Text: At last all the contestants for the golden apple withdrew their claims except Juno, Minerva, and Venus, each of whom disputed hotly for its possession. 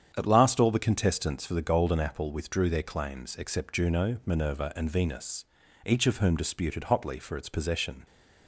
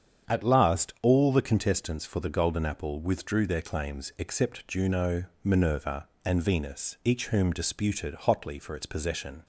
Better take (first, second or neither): first